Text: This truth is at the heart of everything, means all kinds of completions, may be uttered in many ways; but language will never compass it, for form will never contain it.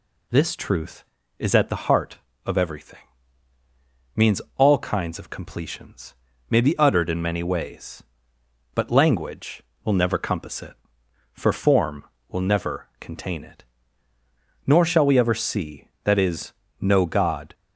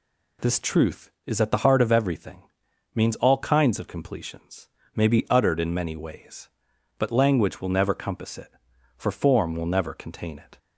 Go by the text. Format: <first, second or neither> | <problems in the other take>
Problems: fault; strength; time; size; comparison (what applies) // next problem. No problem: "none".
second | pauses between "means" and "all"; slight; at 4.4 s; 0.16 s long // goes on to say "Nor shall we ever see that is know God"; strong; from 14.6 s on; 2.8 s long